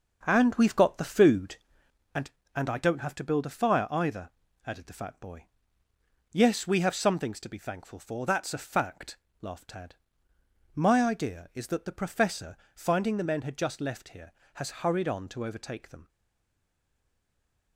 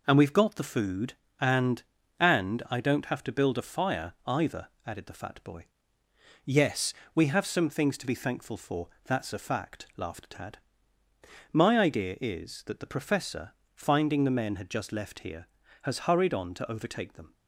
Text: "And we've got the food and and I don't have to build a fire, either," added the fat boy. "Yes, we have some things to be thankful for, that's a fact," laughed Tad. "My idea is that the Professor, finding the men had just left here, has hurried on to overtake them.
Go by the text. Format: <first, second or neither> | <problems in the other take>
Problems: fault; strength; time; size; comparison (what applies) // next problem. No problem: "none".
second | starts louder than the rest; until 1.2 s; 6.5 dB // stays silent after the last word; noticeable; from 16.0 s on; 1.7 s long